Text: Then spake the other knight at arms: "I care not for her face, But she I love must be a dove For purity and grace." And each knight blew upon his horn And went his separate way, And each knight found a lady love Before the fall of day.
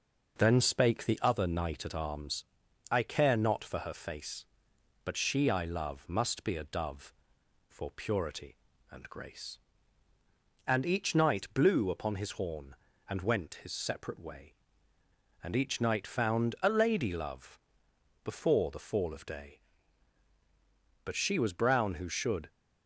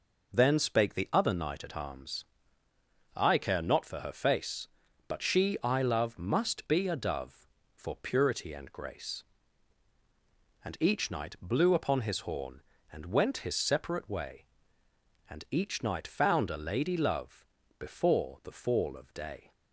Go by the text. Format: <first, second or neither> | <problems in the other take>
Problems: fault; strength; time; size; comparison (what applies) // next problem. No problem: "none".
second | pauses between "love" and "Before"; noticeable; at 17.5 s; 0.64 s long; slight in the second // goes on to say "But she was brown who should"; from 21.0 s on; 1.4 s long